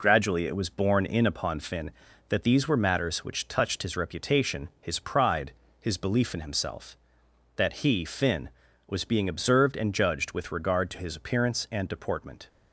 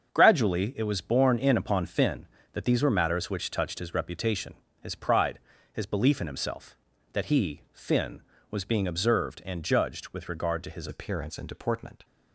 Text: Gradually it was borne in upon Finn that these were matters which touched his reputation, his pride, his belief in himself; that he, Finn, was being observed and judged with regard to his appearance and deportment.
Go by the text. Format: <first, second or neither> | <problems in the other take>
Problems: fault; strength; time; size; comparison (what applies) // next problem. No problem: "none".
first | starts louder than the rest; until 1.1 s; 6.5 dB // changes voice at "appearance"; from 10.8 s on; 1.2 s long